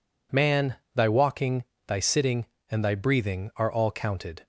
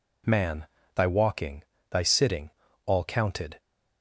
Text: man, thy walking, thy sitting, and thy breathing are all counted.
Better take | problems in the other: first | skips "and thy breathing are"; at 2.6 s

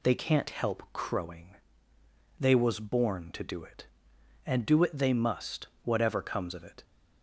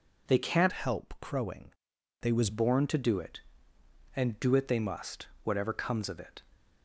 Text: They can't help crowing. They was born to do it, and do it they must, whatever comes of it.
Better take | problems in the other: first | changes voice from "help" to "was"; from 0.7 to 2.4 s; 1.7 s long

